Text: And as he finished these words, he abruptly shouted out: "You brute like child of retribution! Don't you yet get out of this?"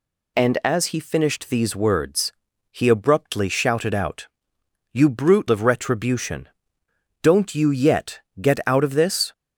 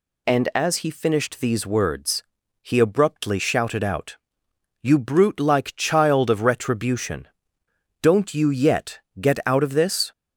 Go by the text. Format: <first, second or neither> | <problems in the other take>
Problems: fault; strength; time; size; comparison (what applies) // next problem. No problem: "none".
second | skips "like child"; at 5.4 s // pauses between "yet" and "get"; slight; at 8.1 s; 0.18 s long; slight in the second